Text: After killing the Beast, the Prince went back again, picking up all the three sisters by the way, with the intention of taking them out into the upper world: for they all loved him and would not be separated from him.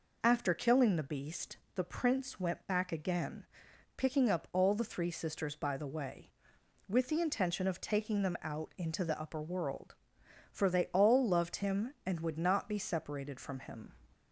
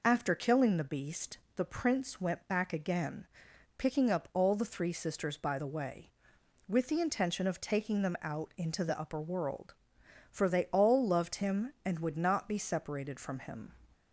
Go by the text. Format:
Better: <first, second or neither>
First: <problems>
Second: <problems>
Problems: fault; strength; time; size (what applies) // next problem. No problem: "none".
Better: neither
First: none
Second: none